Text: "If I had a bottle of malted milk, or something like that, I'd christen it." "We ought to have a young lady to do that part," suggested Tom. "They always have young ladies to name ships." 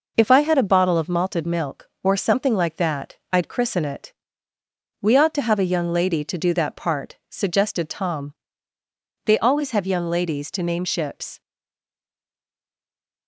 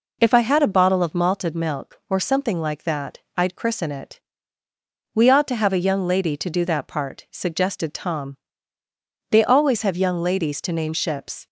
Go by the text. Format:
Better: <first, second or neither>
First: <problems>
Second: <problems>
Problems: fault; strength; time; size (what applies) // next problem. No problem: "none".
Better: second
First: stays silent after the last word; noticeable; from 11.4 s on; 1.8 s long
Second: none